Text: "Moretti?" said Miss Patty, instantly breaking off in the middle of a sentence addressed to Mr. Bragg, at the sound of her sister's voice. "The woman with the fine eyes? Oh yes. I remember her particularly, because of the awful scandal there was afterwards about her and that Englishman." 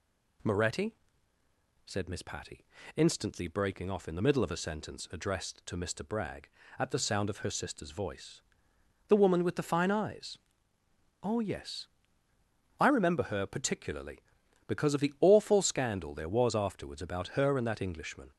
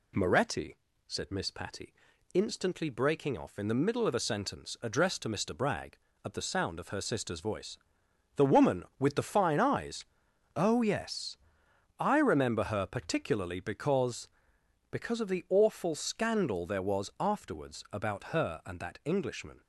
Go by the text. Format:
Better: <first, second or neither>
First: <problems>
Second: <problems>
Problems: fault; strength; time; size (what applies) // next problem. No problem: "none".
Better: first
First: none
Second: says "because" twice; at 14.9 s